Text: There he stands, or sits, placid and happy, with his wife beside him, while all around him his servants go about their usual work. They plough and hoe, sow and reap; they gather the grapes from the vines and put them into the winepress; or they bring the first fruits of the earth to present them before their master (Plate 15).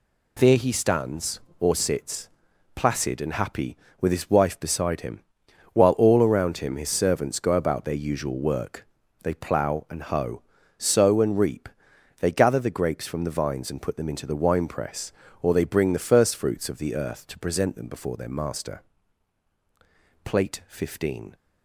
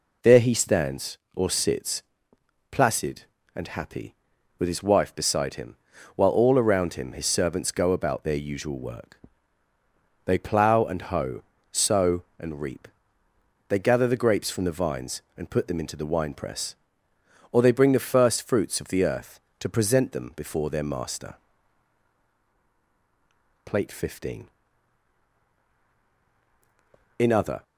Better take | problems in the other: first | goes on to say "In other"; slight; from 27.1 s on; 0.46 s long

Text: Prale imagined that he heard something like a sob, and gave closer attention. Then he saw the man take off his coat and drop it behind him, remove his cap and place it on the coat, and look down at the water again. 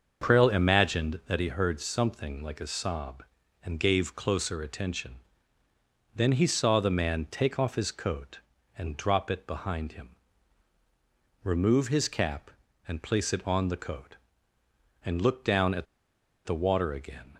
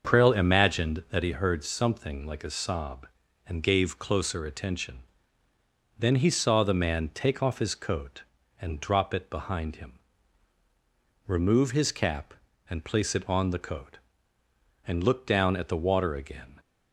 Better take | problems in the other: second | starts louder than the rest; until 1.3 s; 6.5 dB; also in the second // pauses between "at" and "the"; noticeable; at 15.8 s; 0.61 s long

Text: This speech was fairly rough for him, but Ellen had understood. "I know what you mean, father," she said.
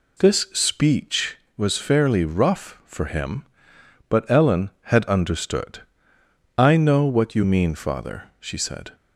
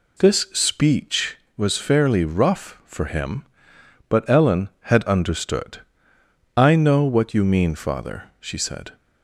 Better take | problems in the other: neither | none

